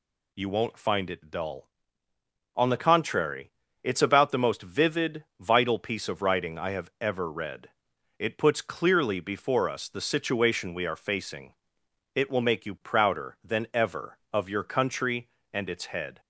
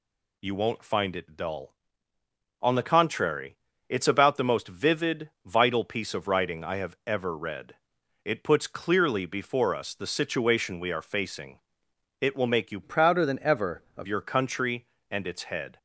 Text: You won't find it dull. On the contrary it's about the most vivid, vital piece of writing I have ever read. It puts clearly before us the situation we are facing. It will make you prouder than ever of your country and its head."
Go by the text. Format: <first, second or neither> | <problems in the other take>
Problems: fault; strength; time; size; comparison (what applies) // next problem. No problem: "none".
first | pauses between "contrary" and "it's"; slight; at 3.5 s; 0.32 s long; slight in the first // changes voice from "prouder" to "of"; from 12.8 to 14.0 s; 1.2 s long